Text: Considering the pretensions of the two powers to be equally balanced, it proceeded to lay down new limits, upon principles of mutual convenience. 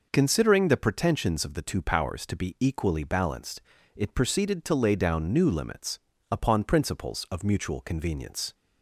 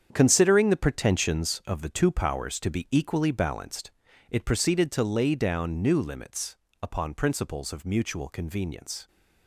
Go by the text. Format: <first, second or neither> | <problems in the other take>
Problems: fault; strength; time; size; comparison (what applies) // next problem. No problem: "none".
first | gets quieter; strong; throughout; 10.5 dB